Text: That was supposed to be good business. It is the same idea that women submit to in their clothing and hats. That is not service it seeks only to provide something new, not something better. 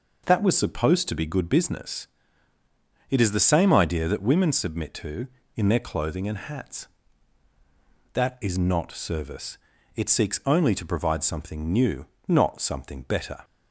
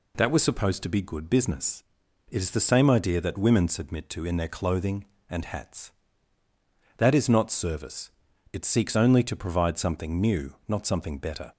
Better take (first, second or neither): neither